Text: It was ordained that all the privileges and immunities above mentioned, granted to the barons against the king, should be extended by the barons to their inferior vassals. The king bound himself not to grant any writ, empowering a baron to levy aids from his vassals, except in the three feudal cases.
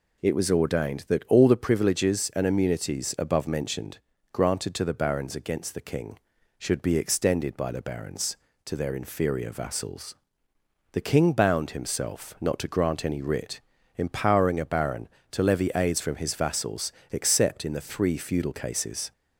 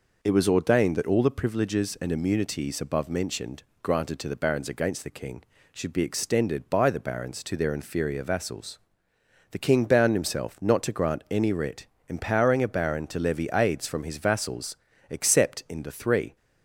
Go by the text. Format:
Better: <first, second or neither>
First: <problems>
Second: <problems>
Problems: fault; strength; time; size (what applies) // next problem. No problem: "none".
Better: first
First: none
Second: stops before "feudal cases"; at 16.3 s